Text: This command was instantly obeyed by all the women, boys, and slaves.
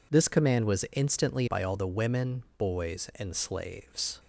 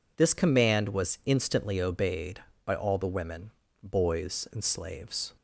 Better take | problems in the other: second | skips "obeyed"; at 1.4 s

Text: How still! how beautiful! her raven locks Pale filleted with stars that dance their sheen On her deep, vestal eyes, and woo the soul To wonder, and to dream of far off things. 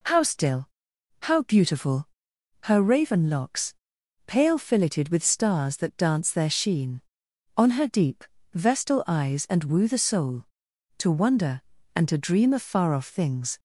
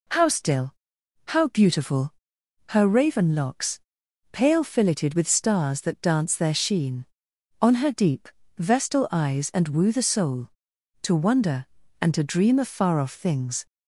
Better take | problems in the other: neither | pauses between "locks" and "Pale"; noticeable; the same in both

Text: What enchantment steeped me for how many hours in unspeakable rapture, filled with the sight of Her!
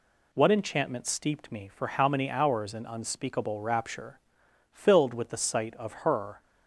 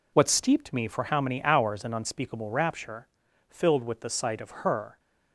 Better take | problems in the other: first | skips "enchantment"; at 0.2 s

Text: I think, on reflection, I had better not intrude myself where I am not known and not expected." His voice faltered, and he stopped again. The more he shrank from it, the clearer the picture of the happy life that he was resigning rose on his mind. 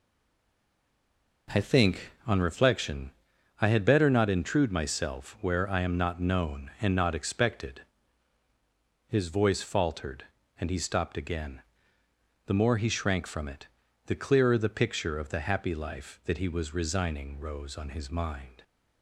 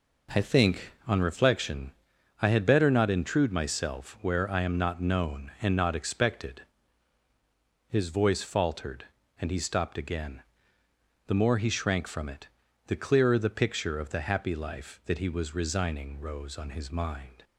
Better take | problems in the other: second | stays silent before the first word; noticeable; until 1.4 s; 1.4 s long

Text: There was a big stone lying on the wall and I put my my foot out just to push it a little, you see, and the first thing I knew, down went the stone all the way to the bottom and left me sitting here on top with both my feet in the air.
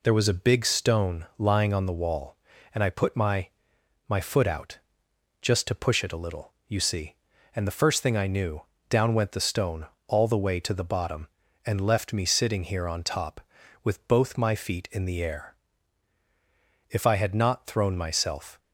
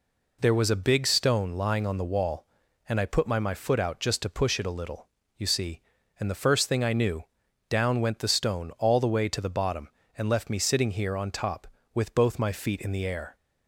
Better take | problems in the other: second | pauses between "my" and "my"; noticeable; at 3.4 s; 0.58 s long // pauses between "out" and "just"; noticeable; at 4.7 s; 0.62 s long // pauses between "stone" and "all"; slight; at 9.8 s; 0.22 s long // goes on to say "If I had not thrown myself"; strong; from 16.8 s on; 1.7 s long

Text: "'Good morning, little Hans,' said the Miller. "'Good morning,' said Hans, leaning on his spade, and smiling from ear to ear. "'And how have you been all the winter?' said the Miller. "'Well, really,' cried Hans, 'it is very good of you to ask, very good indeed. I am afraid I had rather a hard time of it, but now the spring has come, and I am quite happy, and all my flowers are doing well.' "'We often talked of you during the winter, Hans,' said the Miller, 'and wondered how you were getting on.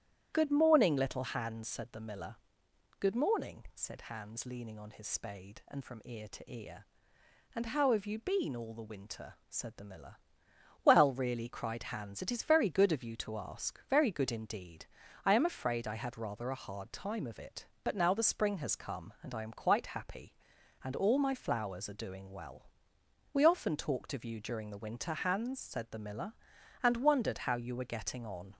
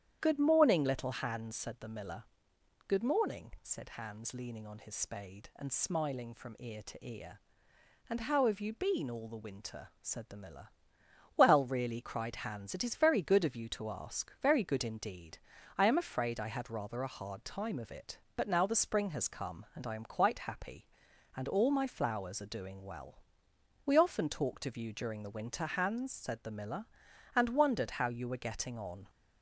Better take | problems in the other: second | starts louder than the rest; strong; until 1.3 s; 10.5 dB; strong in the second // skips "smiling"; at 5.8 s

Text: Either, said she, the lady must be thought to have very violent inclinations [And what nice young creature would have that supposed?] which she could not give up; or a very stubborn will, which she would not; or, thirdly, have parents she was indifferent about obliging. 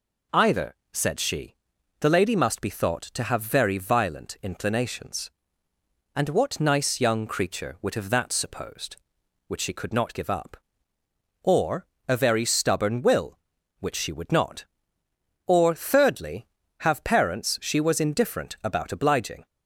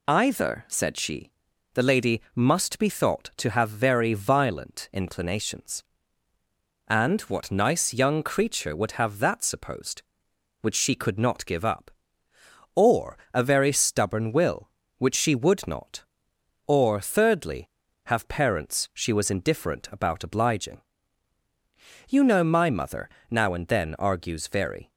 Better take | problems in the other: first | pauses between "or" and "a"; slight; at 13.1 s; 0.16 s long; slight in the first // goes on to say "You know my mother now and then argues very"; strong; from 22.0 s on; 2.8 s long

